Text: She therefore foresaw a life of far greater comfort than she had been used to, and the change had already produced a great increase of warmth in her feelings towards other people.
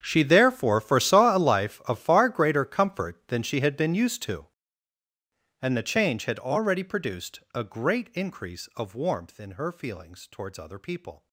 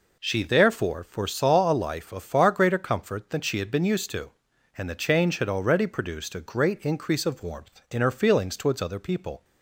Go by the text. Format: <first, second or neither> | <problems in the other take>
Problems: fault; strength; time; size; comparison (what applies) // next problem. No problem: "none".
second | gets quieter; strong; throughout; 20 dB